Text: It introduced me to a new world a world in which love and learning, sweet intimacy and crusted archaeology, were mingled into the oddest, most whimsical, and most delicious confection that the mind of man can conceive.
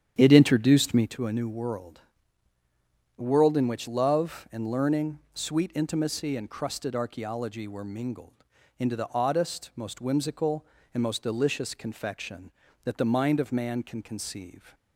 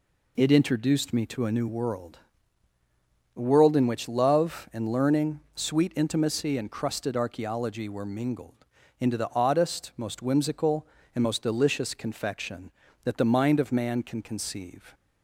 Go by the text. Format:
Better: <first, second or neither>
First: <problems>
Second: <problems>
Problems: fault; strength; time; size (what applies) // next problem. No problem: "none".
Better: second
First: starts louder than the rest; strong; until 1.1 s; 9 dB // pauses between "world" and "a"; at 2.0 s; 1.1 s long // pauses between "mingled" and "into"; slight; at 8.4 s; 0.36 s long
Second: pauses between "world" and "a"; at 2.1 s; 1.1 s long // pauses between "mingled" and "into"; slight; at 8.6 s; 0.36 s long